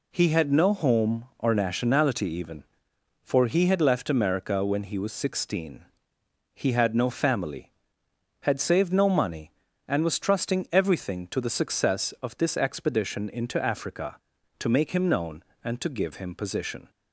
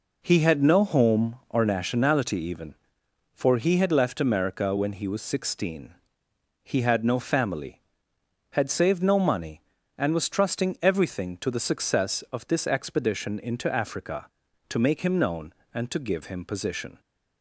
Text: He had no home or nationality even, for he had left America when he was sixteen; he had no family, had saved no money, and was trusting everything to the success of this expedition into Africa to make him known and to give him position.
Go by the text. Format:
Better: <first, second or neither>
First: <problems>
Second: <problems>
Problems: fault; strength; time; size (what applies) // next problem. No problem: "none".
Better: first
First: none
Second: starts louder than the rest; noticeable; until 1.7 s; 4.5 dB